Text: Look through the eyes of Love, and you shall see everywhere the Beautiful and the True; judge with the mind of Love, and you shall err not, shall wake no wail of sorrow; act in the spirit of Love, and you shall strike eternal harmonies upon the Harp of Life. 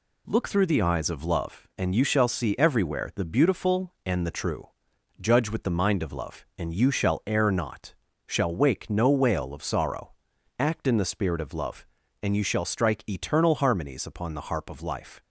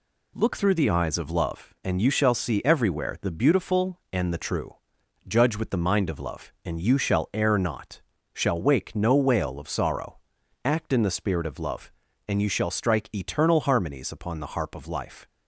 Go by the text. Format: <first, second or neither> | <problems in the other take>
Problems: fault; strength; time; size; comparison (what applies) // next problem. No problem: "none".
neither | none